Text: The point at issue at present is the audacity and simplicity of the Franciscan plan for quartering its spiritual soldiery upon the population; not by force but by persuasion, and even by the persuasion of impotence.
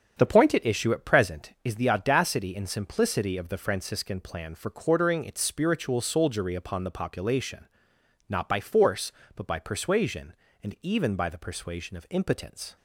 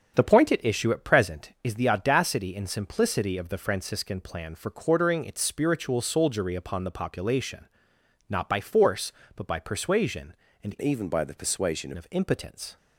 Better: first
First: starts louder than the rest; strong; until 1.2 s; 7.5 dB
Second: starts louder than the rest; until 1.1 s; 7 dB // changes voice from "even" to "persuasion"; from 10.8 to 11.9 s; 1.1 s long

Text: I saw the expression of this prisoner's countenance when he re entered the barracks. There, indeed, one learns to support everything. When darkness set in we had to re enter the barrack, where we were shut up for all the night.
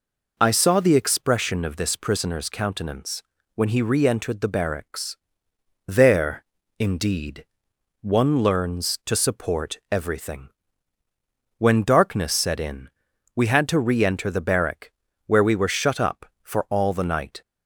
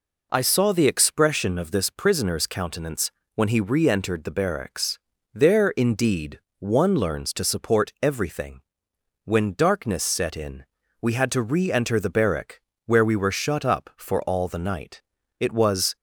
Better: first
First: pauses between "countenance" and "when"; slight; at 3.2 s; 0.32 s long // pauses between "in" and "we"; noticeable; at 12.8 s; 0.46 s long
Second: pauses between "countenance" and "when"; slight; at 3.1 s; 0.24 s long // pauses between "in" and "we"; slight; at 10.6 s; 0.36 s long // goes on to say "It was"; from 15.3 s on; 0.56 s long

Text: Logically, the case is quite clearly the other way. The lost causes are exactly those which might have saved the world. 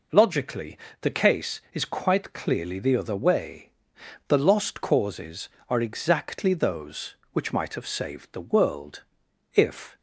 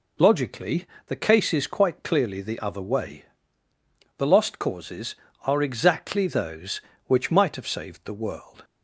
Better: second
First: goes on to say "If"; slight; from 9.5 s on; 0.42 s long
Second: none

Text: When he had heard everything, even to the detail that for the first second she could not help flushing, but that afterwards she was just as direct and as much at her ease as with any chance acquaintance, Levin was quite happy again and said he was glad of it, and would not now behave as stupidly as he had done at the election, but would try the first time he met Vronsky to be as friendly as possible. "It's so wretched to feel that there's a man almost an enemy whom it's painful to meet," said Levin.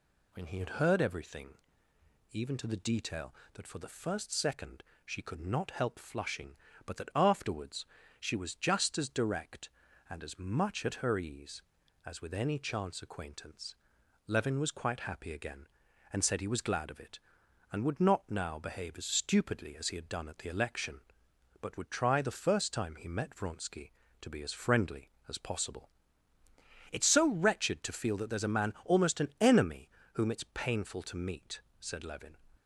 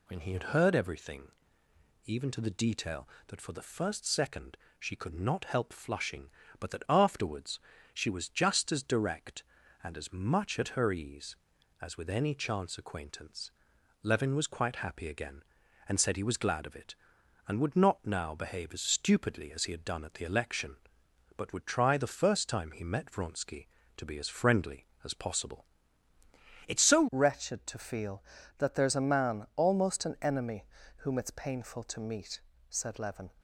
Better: first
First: pauses between "second" and "she"; slight; at 4.8 s; 0.20 s long // pauses between "afterwards" and "she"; slight; at 7.8 s; 0.36 s long // pauses between "enemy" and "whom"; slight; at 29.9 s; 0.24 s long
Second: pauses between "second" and "she"; slight; at 4.5 s; 0.20 s long // pauses between "afterwards" and "she"; slight; at 7.5 s; 0.36 s long // changes voice at "wretched"; from 27.1 s on; 6.2 s long // pauses between "enemy" and "whom"; slight; at 30.6 s; 0.32 s long

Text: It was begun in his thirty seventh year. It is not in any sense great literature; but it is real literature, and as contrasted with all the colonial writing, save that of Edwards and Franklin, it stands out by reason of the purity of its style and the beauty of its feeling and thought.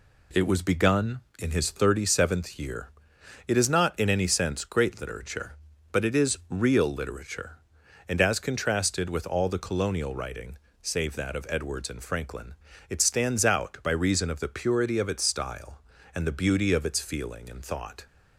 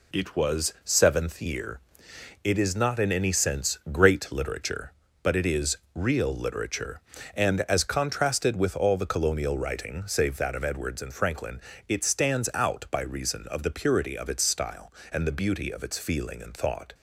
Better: first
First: none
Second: skips "begun in his thirty"; at 0.7 s // pauses between "is" and "real"; slight; at 5.7 s; 0.16 s long

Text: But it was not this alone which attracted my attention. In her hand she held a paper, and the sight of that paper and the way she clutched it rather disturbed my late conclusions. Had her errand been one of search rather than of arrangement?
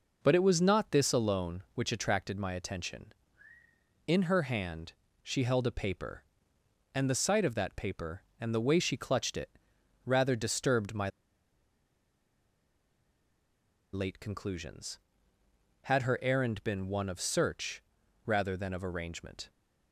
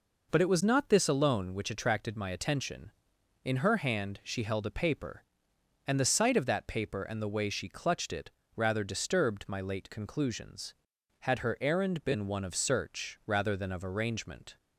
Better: second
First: pauses between "hand" and "she"; slight; at 4.9 s; 0.32 s long // pauses between "it" and "rather"; noticeable; at 9.4 s; 0.56 s long // pauses between "my" and "late"; strong; at 11.0 s; 2.8 s long // pauses between "search" and "rather"; at 17.8 s; 0.42 s long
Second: pauses between "it" and "rather"; slight; at 8.3 s; 0.24 s long

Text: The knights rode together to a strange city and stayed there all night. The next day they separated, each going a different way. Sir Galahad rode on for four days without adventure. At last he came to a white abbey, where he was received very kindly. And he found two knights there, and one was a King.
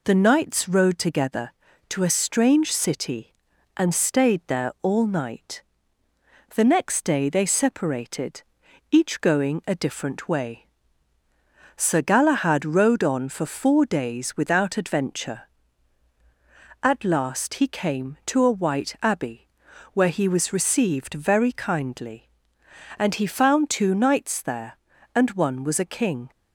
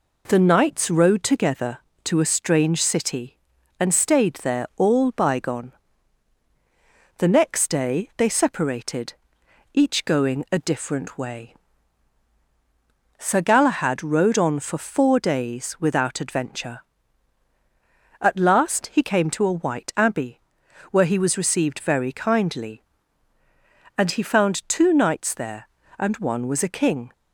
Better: first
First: none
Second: says "bygone" for "night"; at 5.1 s

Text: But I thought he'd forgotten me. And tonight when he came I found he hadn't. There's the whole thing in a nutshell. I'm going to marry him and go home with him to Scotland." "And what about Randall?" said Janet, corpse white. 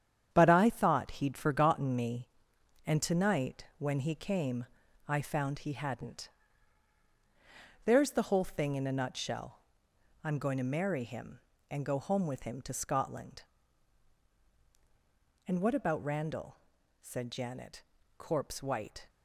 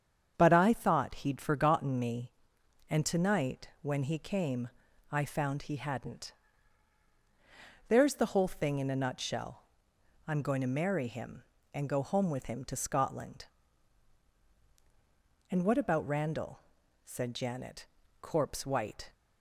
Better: second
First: gets quieter; strong; throughout; 7 dB // starts louder than the rest; strong; until 1.3 s; 9 dB // pauses between "came" and "I"; at 4.6 s; 0.42 s long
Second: starts louder than the rest; strong; until 1.3 s; 8 dB // pauses between "came" and "I"; at 4.6 s; 0.42 s long

